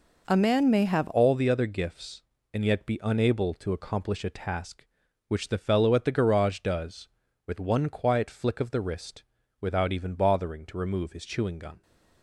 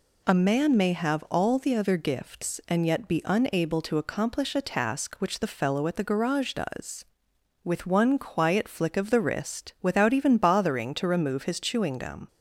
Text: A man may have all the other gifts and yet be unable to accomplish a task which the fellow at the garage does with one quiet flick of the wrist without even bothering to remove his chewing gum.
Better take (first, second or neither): second